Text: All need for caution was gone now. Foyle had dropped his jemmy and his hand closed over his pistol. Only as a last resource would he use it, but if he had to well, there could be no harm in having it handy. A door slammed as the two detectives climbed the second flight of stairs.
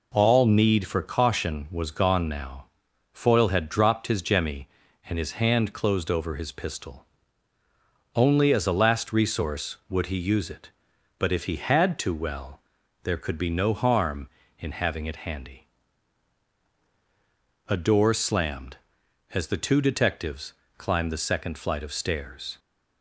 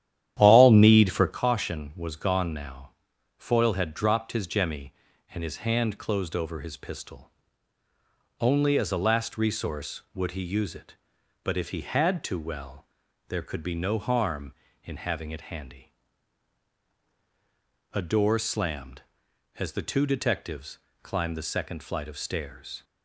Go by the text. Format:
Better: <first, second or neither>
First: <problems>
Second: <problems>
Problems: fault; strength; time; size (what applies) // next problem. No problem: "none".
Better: first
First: pauses between "detectives" and "climbed"; slight; at 20.5 s; 0.24 s long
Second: starts louder than the rest; strong; until 1.4 s; 11 dB // pauses between "detectives" and "climbed"; slight; at 20.7 s; 0.24 s long